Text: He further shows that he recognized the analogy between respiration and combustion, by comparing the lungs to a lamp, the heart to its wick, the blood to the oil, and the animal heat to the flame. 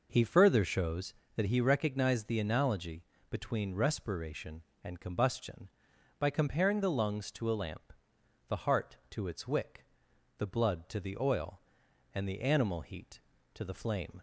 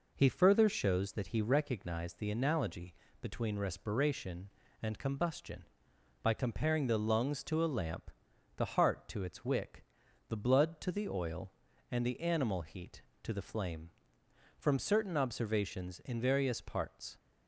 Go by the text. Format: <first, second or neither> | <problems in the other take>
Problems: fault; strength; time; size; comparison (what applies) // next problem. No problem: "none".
first | pauses between "analogy" and "between"; slight; at 2.9 s; 0.26 s long; slight in the first // goes on to say "From certain observations in various parts"; strong; from 14.5 s on; 2.6 s long